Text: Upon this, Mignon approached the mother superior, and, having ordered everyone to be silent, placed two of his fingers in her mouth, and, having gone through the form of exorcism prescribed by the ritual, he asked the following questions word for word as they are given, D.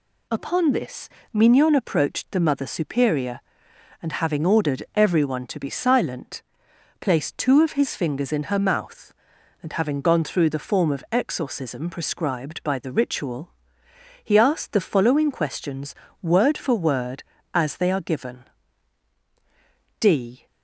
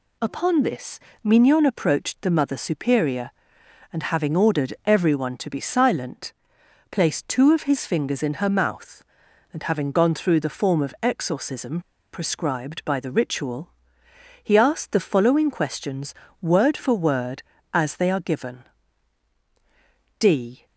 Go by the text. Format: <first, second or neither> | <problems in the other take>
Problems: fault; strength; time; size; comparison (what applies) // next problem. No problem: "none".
first | pauses between "exorcism" and "prescribed"; slight; at 11.8 s; 0.32 s long // pauses between "questions" and "word"; slight; at 16.1 s; 0.28 s long; slight in the first